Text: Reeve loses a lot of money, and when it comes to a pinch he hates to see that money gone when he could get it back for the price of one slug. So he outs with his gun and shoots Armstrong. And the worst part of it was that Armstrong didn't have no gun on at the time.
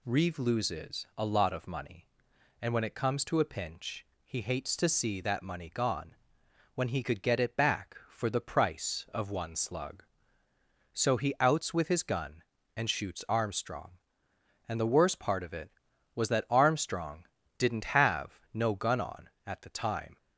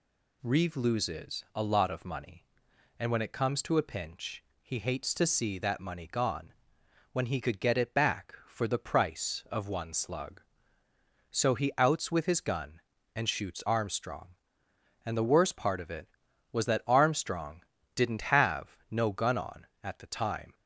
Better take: neither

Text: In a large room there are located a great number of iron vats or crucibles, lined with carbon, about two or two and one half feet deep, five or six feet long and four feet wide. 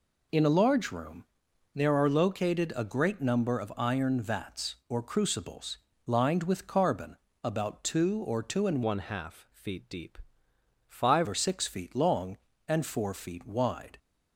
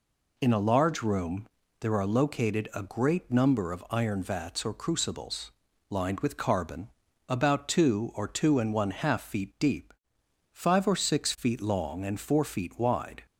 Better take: second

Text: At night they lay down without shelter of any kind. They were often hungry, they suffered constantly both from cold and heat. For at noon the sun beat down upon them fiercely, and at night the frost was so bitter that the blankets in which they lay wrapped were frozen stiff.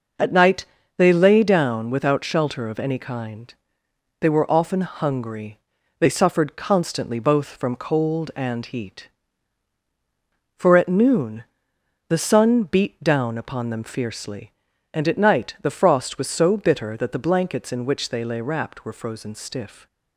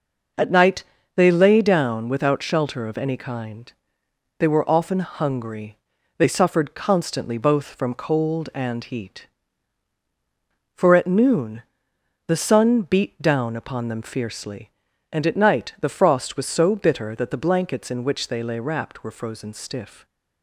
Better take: neither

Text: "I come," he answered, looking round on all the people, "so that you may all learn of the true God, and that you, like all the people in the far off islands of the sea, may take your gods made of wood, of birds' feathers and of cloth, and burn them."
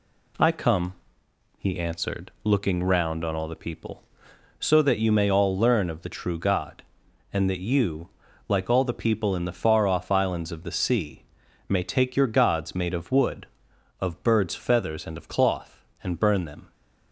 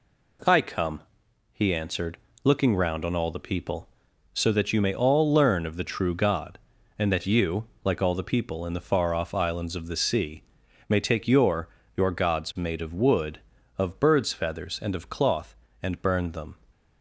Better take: first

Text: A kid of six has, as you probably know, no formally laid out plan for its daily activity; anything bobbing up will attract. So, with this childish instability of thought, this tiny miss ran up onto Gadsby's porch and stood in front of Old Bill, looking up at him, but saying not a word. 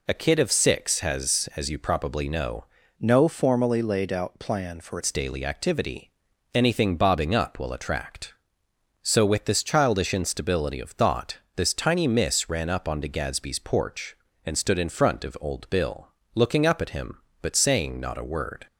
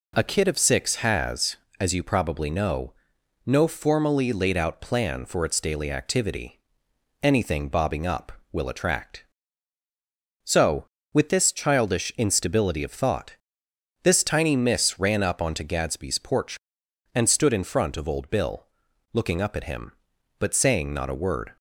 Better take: second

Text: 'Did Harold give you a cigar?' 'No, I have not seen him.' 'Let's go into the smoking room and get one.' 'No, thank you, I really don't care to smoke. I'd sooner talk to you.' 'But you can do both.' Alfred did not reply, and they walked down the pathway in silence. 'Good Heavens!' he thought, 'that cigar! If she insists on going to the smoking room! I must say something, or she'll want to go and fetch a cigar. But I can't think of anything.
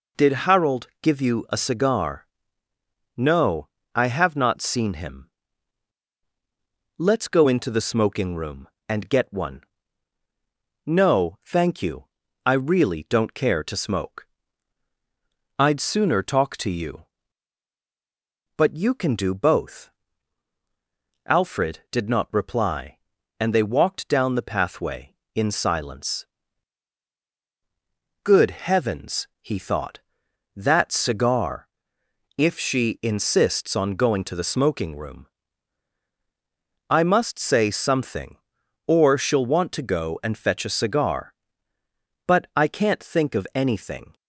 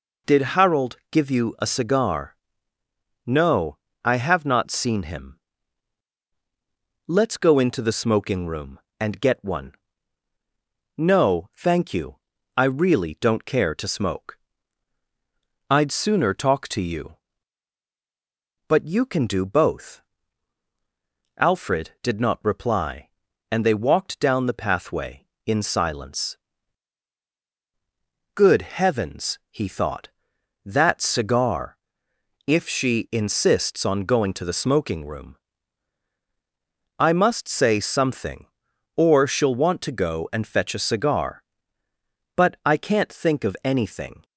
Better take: neither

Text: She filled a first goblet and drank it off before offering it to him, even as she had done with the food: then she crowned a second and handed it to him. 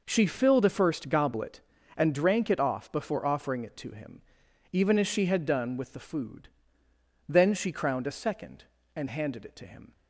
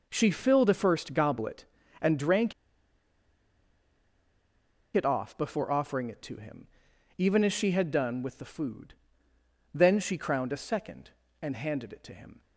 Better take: first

